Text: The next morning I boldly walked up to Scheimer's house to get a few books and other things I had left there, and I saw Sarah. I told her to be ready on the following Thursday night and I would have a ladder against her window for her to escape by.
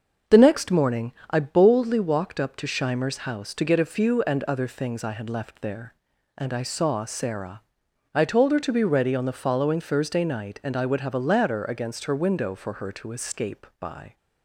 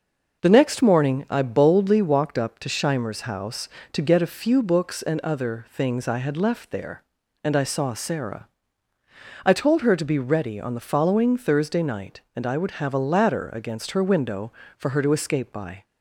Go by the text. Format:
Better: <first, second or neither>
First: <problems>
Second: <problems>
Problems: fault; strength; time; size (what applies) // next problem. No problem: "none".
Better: second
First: starts louder than the rest; until 1.4 s; 6.5 dB // pauses between "morning" and "I"; slight; at 1.1 s; 0.18 s long // skips "books"; at 4.2 s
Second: none